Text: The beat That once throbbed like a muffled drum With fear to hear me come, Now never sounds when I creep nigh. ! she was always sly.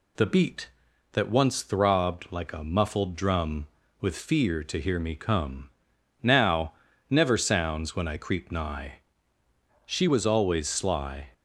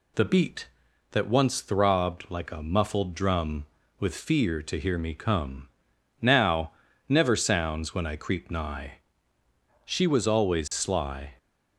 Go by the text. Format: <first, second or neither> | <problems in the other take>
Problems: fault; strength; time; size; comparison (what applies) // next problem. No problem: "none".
neither | pauses between "Now" and "never"; the same in both